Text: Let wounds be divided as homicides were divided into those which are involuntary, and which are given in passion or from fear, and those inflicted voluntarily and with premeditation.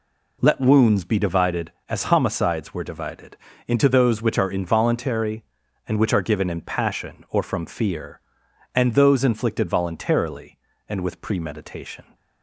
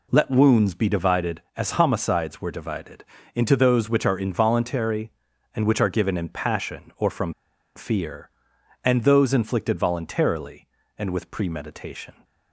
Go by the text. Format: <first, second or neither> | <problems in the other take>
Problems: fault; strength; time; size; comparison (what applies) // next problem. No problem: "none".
first | pauses between "divided" and "into"; slight; at 3.0 s; 0.32 s long; slight in the first // pauses between "from" and "fear"; at 7.3 s; 0.43 s long